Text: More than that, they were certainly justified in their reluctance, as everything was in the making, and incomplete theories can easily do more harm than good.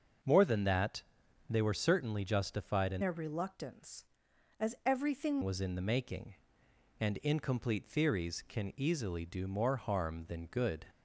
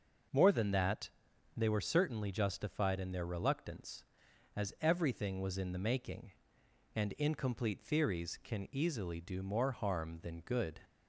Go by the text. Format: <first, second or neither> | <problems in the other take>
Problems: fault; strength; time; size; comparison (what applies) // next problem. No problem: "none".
second | starts louder than the rest; until 1.7 s; 6 dB; noticeable in the second // changes voice from "their" to "everything"; from 3.0 to 5.4 s; 2.4 s long